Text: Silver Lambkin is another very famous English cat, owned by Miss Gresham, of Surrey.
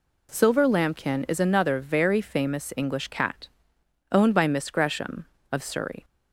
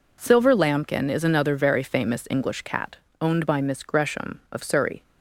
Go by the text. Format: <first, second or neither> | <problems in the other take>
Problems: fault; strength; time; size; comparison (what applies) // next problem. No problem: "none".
neither | none